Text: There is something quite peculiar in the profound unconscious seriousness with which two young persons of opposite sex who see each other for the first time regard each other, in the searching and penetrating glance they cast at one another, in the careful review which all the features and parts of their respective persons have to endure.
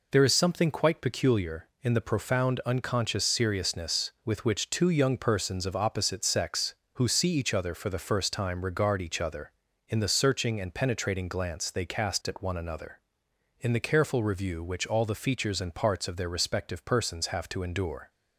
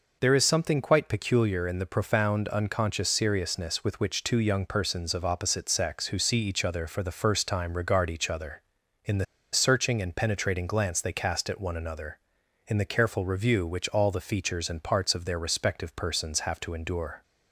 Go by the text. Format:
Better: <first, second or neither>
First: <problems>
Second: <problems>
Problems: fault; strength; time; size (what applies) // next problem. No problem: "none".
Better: first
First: none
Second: pauses between "the" and "searching"; slight; at 9.2 s; 0.27 s long